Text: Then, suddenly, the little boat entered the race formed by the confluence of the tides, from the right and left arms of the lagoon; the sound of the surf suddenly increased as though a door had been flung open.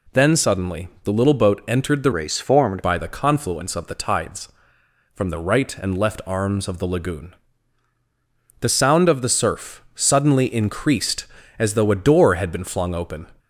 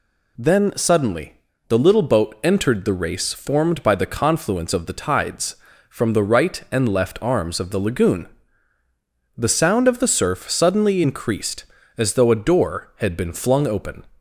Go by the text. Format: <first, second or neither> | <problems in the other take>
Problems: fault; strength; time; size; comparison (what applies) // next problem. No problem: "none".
second | changes voice from "race" to "formed"; from 2.1 to 2.8 s; 0.7 s long